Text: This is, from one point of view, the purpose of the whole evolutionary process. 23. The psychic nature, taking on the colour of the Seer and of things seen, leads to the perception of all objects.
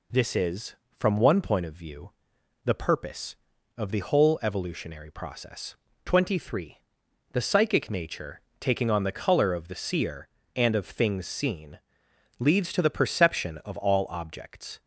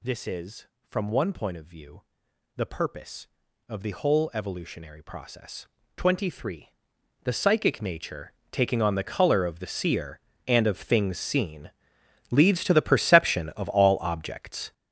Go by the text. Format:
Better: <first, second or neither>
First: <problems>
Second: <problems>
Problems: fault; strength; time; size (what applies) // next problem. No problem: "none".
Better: first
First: none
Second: gets louder; strong; throughout; 10 dB